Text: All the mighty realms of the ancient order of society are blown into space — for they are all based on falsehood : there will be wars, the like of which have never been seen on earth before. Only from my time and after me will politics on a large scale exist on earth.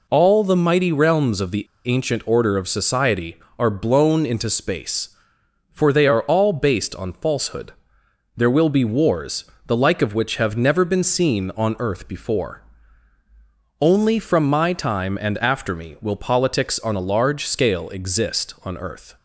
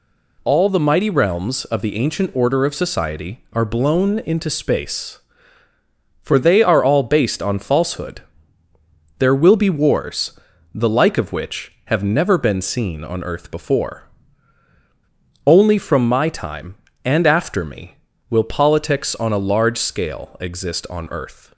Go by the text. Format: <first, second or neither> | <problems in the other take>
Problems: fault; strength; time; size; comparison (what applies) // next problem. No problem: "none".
second | pauses between "the" and "ancient"; slight; at 1.6 s; 0.20 s long